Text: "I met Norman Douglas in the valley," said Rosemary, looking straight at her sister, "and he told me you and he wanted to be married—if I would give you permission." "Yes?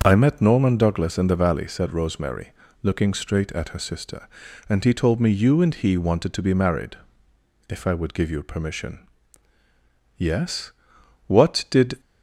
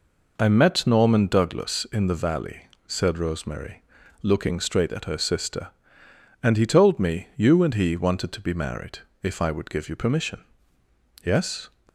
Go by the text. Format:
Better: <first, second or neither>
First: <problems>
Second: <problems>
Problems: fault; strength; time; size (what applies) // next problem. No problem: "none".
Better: second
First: starts louder than the rest; until 1.0 s; 7 dB // goes on to say "What did"; noticeable; from 11.2 s on; 0.72 s long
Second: none